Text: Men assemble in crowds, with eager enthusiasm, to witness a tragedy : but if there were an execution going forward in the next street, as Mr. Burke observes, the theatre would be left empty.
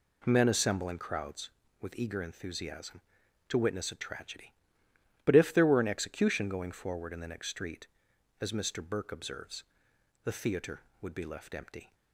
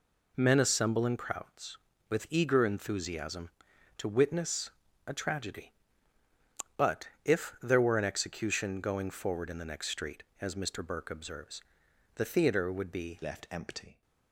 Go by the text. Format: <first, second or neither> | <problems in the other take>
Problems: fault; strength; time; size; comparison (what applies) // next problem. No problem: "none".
first | pauses between "witness" and "a"; slight; at 4.7 s; 0.36 s long // pauses between "but" and "if"; slight; at 7.0 s; 0.16 s long // changes voice at "left"; from 13.2 s on; 0.8 s long